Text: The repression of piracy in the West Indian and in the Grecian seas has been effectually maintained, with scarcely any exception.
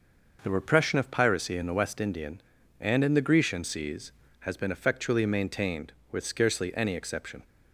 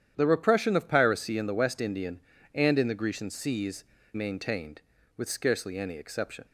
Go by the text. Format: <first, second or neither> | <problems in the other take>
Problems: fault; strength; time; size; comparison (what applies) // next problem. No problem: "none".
first | starts louder than the rest; strong; until 1.1 s; 10 dB // skips "has been effectually"; at 3.9 s